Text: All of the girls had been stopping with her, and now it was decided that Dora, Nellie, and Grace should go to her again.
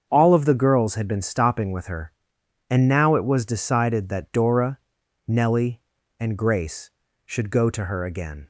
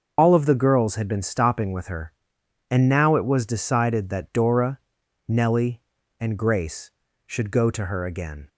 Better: first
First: starts louder than the rest; until 1.1 s; 7 dB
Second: loses the start of "All"; at 0.1 s; 85 ms // starts louder than the rest; noticeable; until 1.1 s; 6 dB

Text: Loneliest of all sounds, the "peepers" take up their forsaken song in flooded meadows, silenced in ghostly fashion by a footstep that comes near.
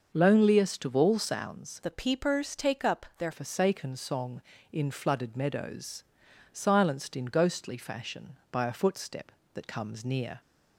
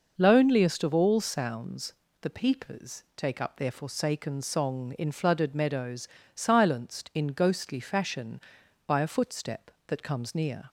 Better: second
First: starts louder than the rest; noticeable; until 1.1 s; 6 dB // changes voice from "the" to "their"; from 1.8 to 3.3 s; 1.5 s long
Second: none

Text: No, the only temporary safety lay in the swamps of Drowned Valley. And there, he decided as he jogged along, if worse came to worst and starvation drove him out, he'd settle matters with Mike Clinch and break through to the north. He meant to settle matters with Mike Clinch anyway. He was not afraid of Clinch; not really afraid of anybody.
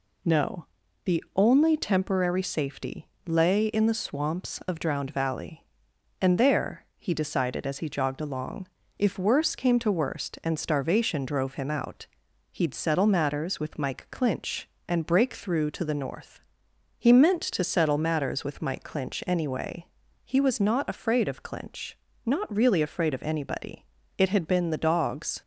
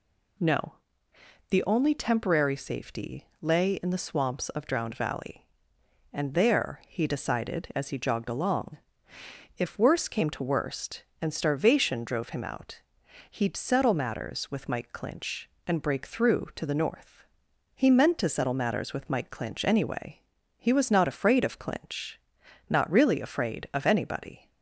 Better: second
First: pauses between "safety" and "lay"; slight; at 3.0 s; 0.18 s long // goes on to say "It had been the dogs"; noticeable; from 24.1 s on; 1.2 s long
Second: none

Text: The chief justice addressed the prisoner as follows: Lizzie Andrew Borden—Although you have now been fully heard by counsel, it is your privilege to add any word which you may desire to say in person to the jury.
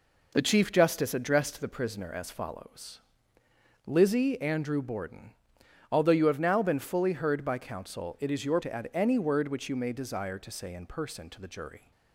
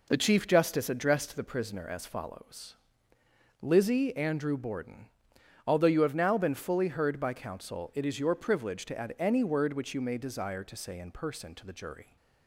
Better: second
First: skips "privilege"; at 8.6 s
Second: none

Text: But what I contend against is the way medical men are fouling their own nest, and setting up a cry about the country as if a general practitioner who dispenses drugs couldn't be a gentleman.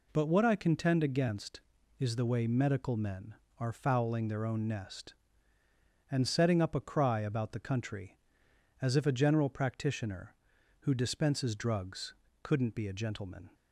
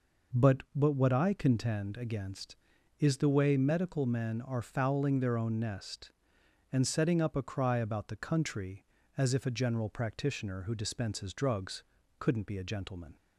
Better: first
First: pauses between "drugs" and "couldn't"; slight; at 12.1 s; 0.28 s long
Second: says "But" twice; at 0.7 s // pauses between "drugs" and "couldn't"; slight; at 11.8 s; 0.34 s long

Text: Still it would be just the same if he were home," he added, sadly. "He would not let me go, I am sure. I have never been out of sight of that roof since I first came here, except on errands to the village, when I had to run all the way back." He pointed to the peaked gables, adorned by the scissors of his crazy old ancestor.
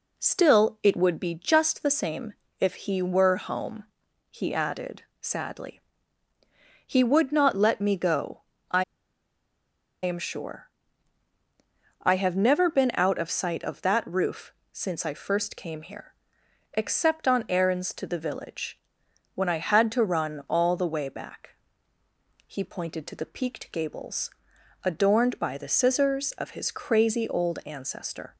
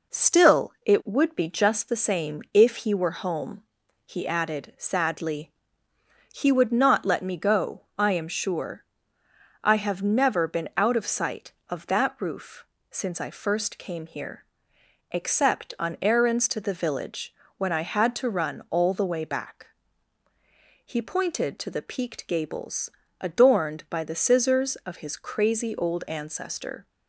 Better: second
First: pauses between "same" and "if"; slight; at 2.3 s; 0.26 s long // pauses between "I" and "am"; at 8.8 s; 1.1 s long // pauses between "roof" and "since"; slight; at 14.5 s; 0.18 s long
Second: pauses between "roof" and "since"; slight; at 12.6 s; 0.26 s long

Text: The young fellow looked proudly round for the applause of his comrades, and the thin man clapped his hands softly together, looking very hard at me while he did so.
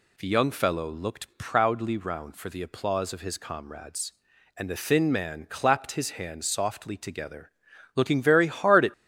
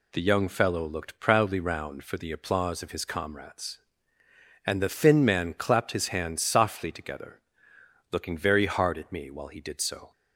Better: second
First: stops before "me while he did so"; at 8.9 s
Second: none

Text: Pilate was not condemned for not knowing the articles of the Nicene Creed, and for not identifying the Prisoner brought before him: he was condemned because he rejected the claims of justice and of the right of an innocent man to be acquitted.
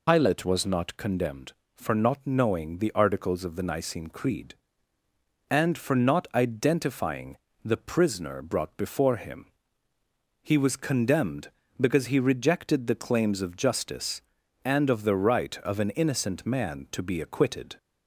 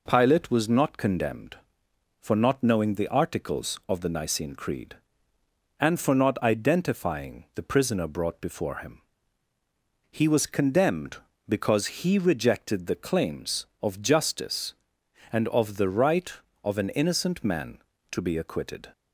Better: second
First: loses the start of "Pilate"; at 0.0 s; 90 ms // pauses between "identifying" and "the"; slight; at 7.3 s; 0.26 s long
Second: none

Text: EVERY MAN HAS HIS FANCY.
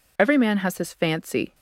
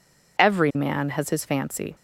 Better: neither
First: none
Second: none

